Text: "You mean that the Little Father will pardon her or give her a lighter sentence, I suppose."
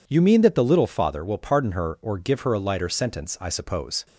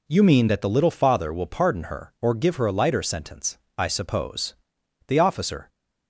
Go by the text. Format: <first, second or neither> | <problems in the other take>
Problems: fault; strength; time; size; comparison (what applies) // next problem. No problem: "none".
first | goes on to say "The officer"; from 5.0 s on; 0.60 s long